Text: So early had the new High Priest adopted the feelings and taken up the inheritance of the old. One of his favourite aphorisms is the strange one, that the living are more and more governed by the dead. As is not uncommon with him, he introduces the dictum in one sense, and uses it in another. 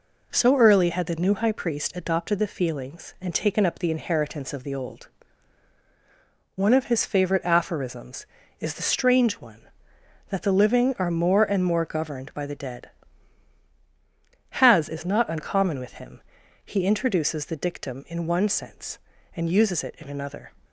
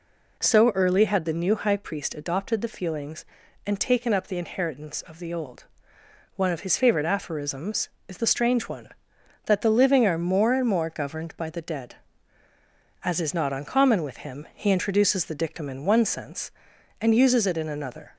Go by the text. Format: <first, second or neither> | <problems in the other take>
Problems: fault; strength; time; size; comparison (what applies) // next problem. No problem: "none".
second | says "Has" for "As"; at 14.6 s